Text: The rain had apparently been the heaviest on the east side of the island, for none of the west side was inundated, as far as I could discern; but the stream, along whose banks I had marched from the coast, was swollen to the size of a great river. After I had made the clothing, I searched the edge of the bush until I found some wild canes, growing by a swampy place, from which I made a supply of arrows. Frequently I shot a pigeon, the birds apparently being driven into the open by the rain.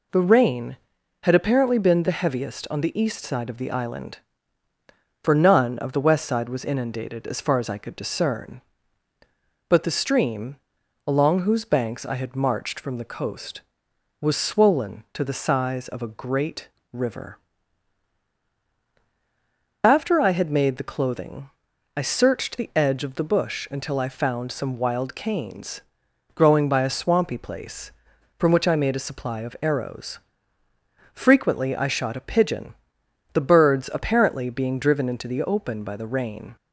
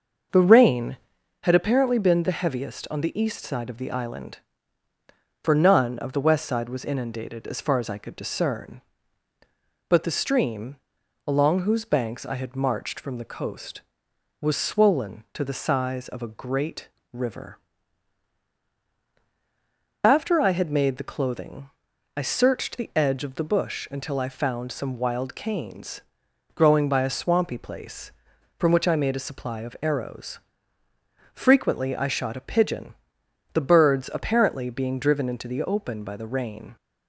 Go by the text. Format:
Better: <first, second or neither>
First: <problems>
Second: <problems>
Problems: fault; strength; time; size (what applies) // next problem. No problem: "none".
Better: first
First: pauses between "great" and "river"; slight; at 16.6 s; 0.22 s long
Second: starts louder than the rest; until 1.4 s; 6 dB // pauses between "great" and "river"; slight; at 16.8 s; 0.22 s long